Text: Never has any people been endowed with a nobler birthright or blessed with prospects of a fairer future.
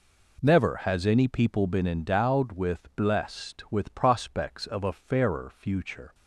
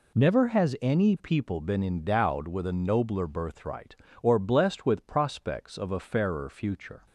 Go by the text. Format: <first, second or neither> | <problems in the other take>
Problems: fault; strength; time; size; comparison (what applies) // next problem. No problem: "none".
second | skips "a nobler birthright or"; at 2.9 s